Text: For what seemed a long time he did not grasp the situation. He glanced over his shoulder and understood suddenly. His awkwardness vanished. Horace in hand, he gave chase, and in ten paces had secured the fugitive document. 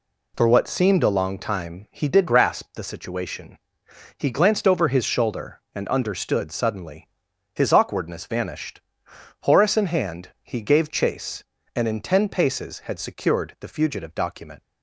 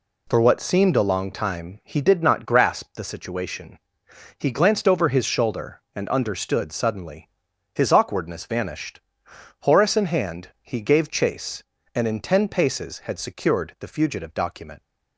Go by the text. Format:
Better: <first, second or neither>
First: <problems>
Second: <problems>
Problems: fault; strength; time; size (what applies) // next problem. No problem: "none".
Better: second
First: skips "not"; at 2.2 s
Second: none